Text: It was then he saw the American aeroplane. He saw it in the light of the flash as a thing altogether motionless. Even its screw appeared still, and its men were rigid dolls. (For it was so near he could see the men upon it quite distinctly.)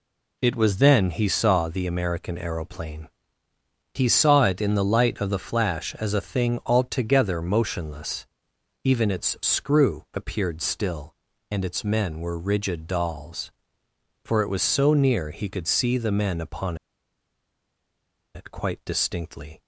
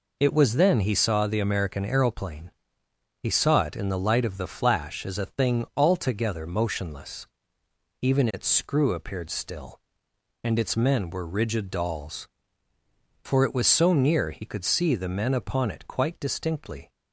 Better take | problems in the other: second | pauses between "upon" and "it"; strong; at 16.7 s; 1.5 s long

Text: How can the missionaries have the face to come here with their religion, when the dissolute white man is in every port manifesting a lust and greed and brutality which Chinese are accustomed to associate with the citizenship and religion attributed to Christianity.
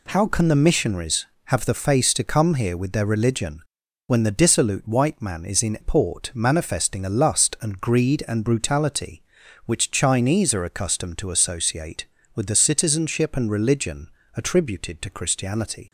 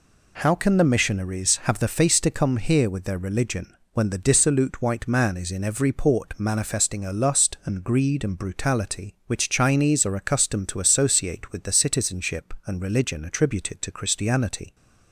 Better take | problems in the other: second | skips "every"; at 5.7 s // pauses between "religion" and "attributed"; slight; at 14.0 s; 0.28 s long

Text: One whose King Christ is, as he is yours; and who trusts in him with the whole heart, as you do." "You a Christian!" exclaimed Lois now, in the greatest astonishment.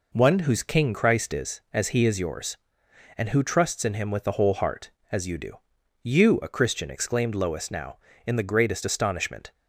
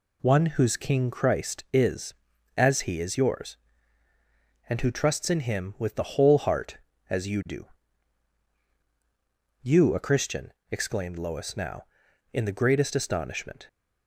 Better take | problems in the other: neither | none

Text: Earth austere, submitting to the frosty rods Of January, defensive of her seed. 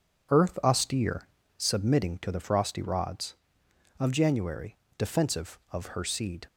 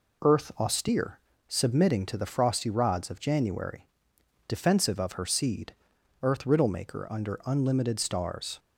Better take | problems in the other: first | goes on to say "Earth riddle maker under unlimited Stars"; strong; from 6.2 s on; 2.3 s long

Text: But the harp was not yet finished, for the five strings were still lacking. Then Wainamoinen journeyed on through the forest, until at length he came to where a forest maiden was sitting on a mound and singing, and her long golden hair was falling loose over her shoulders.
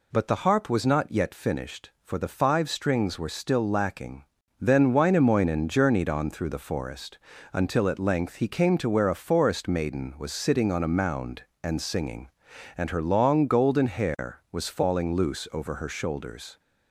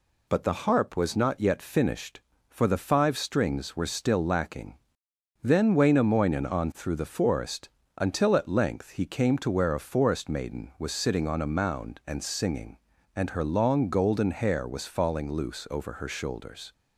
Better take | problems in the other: first | skips "journeyed"; at 6.4 s

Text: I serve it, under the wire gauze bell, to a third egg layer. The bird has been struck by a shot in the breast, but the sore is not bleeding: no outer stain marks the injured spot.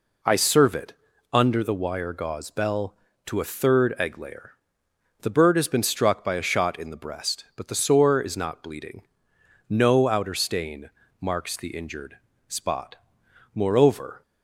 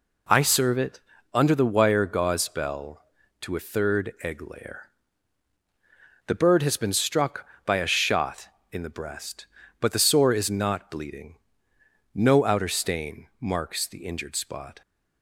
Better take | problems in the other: second | pauses between "stain" and "marks"; slight; at 10.8 s; 0.30 s long // pauses between "injured" and "spot"; slight; at 12.1 s; 0.30 s long // goes on to say "Moreover"; noticeable; from 13.5 s on; 0.70 s long

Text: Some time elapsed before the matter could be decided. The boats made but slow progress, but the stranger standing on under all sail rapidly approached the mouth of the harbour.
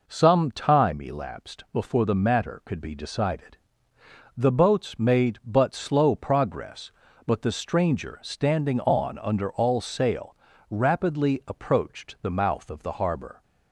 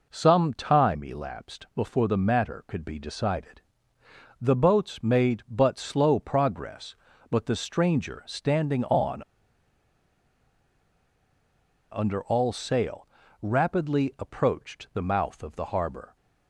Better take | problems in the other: first | pauses between "on" and "under"; strong; at 9.2 s; 2.6 s long // pauses between "sail" and "rapidly"; slight; at 13.0 s; 0.36 s long; slight in the first

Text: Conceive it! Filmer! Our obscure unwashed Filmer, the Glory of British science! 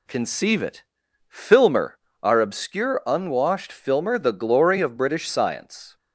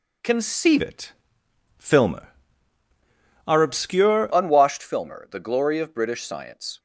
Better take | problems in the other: first | changes voice from "it" to "obscure"; from 0.8 to 4.3 s; 3.5 s long

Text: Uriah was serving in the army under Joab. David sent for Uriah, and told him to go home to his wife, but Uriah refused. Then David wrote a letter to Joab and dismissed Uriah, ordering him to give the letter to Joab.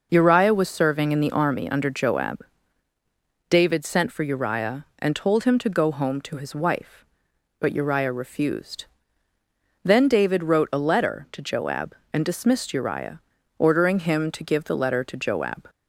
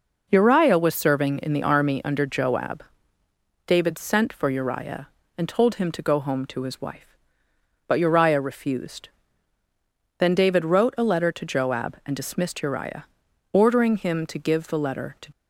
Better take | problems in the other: first | stops before "Joab"; at 15.3 s

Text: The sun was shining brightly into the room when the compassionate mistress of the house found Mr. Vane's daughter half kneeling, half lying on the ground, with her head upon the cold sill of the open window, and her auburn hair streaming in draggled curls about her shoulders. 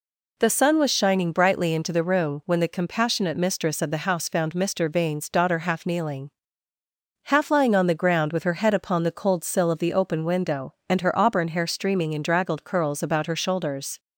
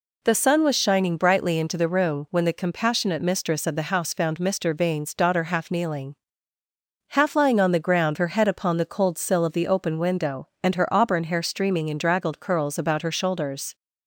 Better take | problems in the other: first | skips "with"; at 8.1 s

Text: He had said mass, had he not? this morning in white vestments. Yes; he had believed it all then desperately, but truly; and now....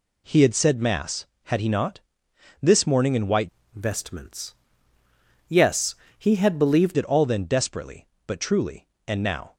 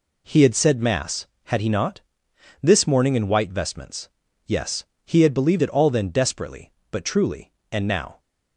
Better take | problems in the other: second | changes voice from "vestments" to "believed"; from 3.7 to 6.9 s; 3.2 s long

